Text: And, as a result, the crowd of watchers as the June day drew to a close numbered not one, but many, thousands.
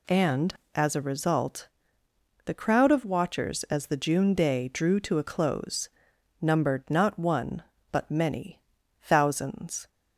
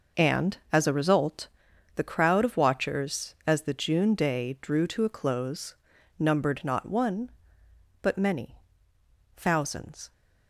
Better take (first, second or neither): neither